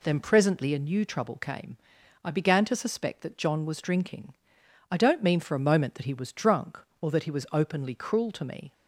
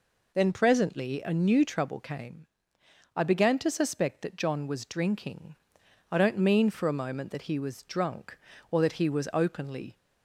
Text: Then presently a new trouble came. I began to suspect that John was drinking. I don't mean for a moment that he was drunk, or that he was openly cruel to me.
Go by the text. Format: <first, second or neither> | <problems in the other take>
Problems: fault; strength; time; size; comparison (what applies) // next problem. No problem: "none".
first | stops before "cruel to me"; at 9.9 s